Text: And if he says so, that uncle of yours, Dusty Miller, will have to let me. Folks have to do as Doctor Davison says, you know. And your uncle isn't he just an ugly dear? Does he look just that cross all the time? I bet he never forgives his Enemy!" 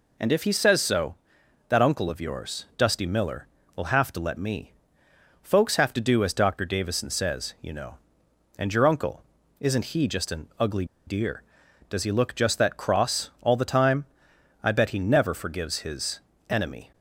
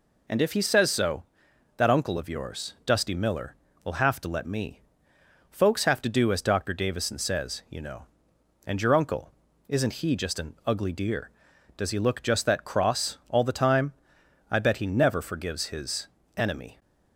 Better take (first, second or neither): second